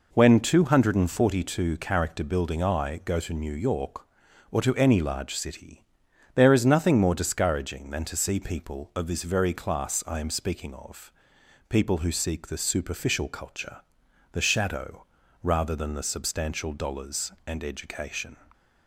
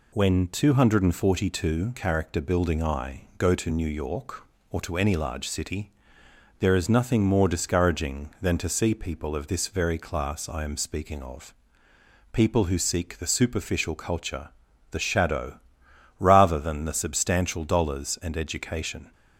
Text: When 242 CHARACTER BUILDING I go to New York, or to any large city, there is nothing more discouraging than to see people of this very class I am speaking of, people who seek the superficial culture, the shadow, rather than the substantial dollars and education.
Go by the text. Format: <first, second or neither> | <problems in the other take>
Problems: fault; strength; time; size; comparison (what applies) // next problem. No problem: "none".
neither | none